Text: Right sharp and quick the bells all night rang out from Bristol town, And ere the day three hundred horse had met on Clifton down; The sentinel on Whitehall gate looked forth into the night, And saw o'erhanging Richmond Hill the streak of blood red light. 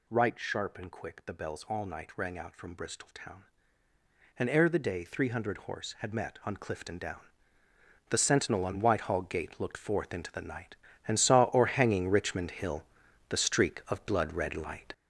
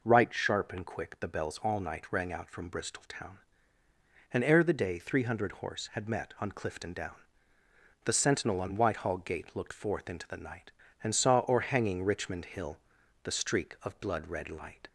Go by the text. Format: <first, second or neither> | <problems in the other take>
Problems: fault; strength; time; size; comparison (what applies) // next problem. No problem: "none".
second | gets louder; strong; throughout; 7.5 dB // pauses between "Hill" and "the"; noticeable; at 12.8 s; 0.46 s long; noticeable in the second